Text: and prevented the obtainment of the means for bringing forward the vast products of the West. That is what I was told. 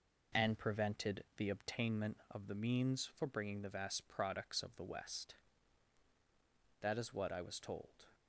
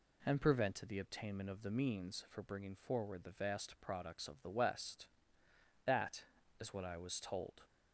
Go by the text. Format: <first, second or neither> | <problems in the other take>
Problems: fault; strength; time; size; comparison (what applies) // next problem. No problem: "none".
second | skips "forward"; at 3.6 s